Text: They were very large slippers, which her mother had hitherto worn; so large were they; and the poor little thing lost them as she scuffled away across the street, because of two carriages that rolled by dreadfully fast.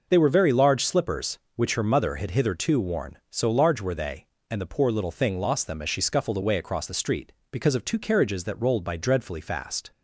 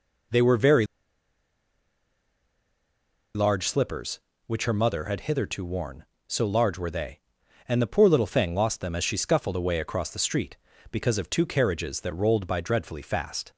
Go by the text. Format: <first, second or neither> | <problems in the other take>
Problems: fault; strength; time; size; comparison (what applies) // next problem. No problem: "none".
first | pauses between "very" and "large"; strong; at 0.8 s; 2.4 s long